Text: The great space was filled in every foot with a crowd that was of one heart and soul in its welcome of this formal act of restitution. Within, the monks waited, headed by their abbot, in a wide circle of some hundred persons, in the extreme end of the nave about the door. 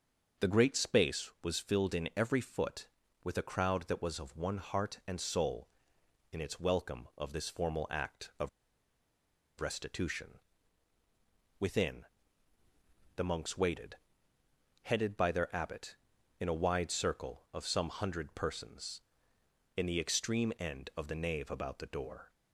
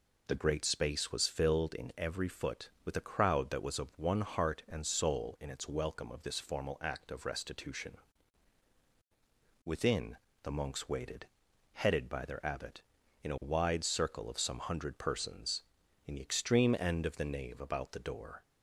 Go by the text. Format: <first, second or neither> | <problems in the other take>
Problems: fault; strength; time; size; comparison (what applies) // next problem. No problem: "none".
second | starts louder than the rest; until 1.5 s; 6 dB // pauses between "of" and "restitution"; at 8.4 s; 1.1 s long